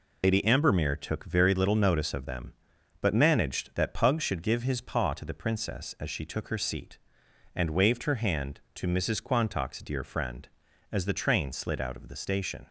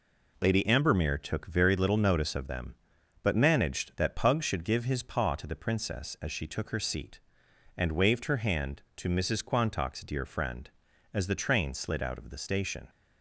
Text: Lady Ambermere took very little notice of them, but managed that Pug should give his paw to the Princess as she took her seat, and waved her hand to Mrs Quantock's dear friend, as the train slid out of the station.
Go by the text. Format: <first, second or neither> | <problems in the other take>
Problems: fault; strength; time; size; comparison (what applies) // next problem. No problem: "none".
second | loses the start of "Lady"; at 0.2 s; 90 ms